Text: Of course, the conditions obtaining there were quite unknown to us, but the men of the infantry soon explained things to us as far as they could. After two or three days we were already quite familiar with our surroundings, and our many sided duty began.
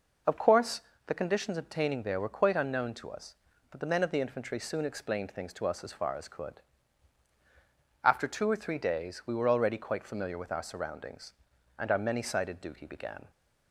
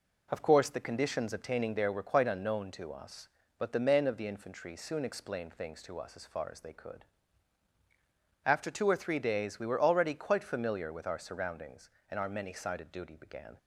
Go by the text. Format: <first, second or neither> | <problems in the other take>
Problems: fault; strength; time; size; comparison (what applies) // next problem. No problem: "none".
second | skips "they"; at 6.2 s